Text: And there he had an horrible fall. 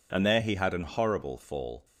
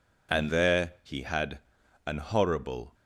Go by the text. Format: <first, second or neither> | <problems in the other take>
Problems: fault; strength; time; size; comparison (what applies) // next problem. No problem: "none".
first | pauses between "had" and "an"; noticeable; at 1.5 s; 0.48 s long // stops before "fall"; at 2.9 s